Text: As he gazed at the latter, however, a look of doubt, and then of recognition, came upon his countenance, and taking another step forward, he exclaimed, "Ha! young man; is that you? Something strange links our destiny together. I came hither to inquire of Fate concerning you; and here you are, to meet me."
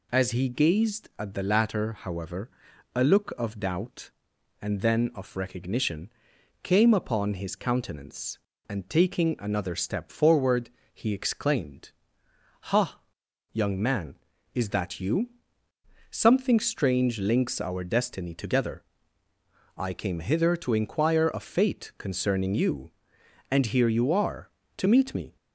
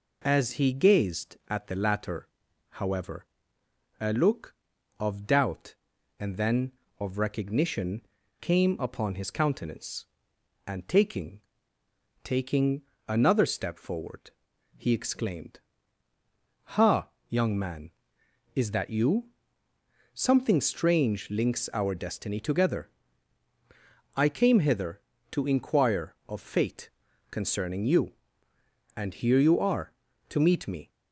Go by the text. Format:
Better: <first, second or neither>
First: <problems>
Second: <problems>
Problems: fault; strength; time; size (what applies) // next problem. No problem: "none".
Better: first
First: none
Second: says "taking" twice; at 12.2 s // pauses between "Fate" and "concerning"; at 26.9 s; 0.40 s long